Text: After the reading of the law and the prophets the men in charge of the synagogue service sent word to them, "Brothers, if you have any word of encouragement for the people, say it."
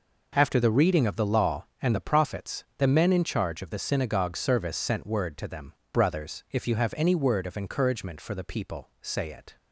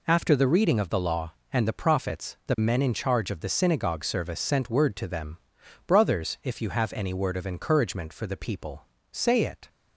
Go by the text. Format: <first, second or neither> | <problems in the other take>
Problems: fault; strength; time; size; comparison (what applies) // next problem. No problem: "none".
neither | none